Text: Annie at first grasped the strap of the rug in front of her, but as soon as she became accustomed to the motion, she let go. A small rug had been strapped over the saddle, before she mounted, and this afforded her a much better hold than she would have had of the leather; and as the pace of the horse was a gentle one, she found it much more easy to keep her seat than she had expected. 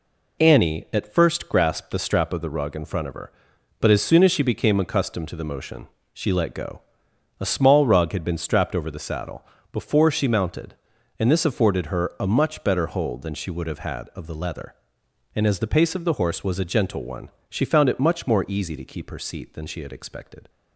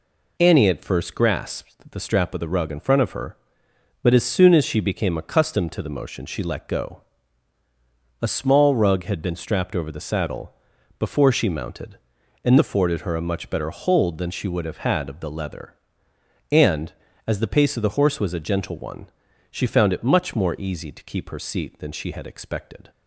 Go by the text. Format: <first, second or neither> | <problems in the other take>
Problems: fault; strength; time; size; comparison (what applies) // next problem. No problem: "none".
first | skips "this"; at 12.5 s